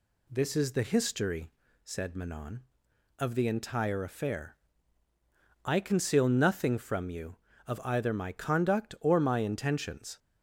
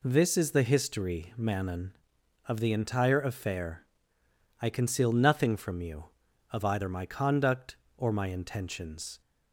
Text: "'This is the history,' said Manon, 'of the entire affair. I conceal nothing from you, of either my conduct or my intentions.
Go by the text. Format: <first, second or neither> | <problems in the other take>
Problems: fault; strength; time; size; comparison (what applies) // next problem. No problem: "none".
first | skips "said"; at 1.3 s